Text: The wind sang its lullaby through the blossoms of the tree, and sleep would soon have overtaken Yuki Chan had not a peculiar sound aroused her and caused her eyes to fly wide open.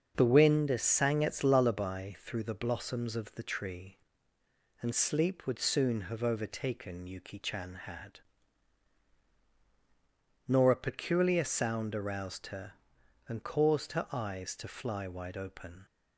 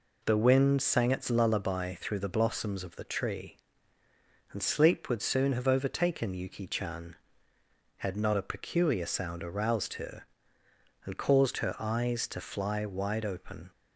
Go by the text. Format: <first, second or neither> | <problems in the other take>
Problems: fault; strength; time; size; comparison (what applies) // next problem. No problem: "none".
second | starts louder than the rest; until 1.2 s; 6.5 dB // says "nor" for "not"; at 10.4 s